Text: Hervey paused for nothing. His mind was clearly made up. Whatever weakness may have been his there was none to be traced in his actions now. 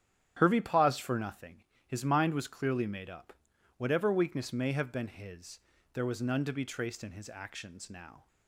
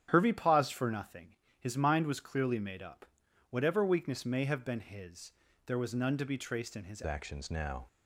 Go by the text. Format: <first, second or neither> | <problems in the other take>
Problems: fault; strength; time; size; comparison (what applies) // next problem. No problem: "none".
first | starts louder than the rest; strong; until 1.1 s; 9.5 dB; strong in the first // pauses between "his" and "there"; at 5.2 s; 0.38 s long; also in the first // changes voice at "actions"; from 7.0 s on; 0.8 s long